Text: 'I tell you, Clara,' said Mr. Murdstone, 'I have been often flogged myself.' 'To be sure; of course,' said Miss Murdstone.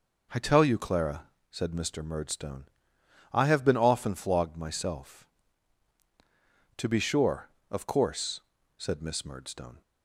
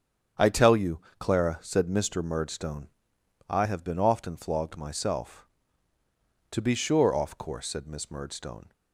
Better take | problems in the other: first | starts louder than the rest; strong; until 1.5 s; 8 dB // says "off" for "of"; at 7.1 s

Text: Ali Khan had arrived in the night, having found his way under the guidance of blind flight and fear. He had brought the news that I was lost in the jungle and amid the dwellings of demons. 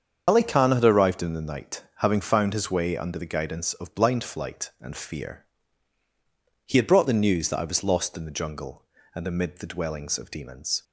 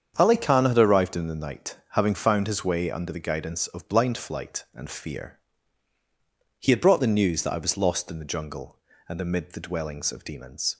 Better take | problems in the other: second | loses the start of "Ali"; at 0.2 s; 65 ms // starts louder than the rest; strong; until 1.2 s; 7 dB; strong in the second

